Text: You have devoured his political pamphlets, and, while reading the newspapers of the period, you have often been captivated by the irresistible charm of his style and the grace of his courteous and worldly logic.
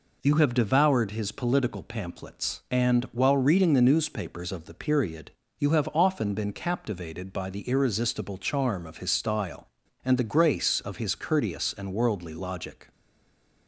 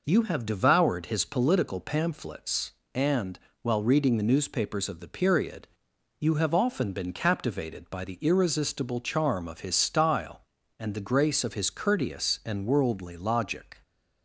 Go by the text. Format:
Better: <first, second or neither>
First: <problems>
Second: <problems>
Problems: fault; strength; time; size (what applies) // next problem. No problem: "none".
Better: second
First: stays silent after the last word; slight; from 12.9 s on; 0.7 s long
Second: none